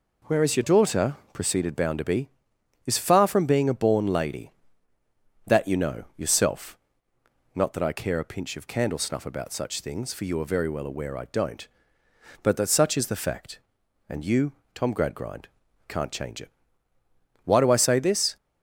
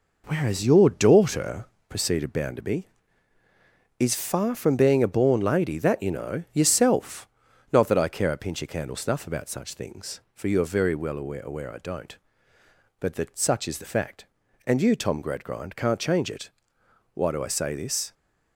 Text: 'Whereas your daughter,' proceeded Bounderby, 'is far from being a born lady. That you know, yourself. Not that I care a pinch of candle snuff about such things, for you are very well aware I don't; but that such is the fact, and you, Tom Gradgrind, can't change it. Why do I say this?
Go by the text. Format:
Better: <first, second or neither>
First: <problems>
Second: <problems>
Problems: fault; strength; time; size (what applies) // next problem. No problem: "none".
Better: first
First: none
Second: says "aware" twice; at 11.4 s